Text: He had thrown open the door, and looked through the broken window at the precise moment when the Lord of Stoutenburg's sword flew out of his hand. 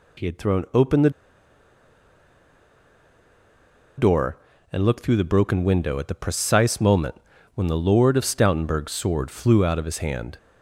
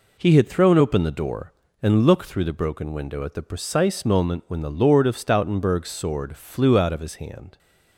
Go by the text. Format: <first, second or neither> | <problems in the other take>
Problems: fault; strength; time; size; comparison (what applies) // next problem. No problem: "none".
second | pauses between "the" and "door"; strong; at 1.1 s; 2.8 s long // pauses between "moment" and "when"; at 7.1 s; 0.38 s long